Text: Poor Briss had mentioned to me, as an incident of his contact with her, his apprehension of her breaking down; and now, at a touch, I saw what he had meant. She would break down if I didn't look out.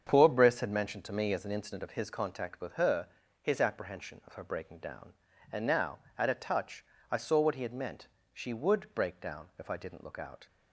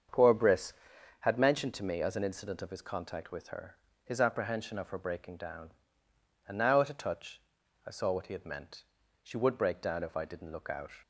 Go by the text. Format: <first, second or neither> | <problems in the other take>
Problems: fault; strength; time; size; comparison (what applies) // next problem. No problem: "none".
neither | starts louder than the rest; strong; the same in both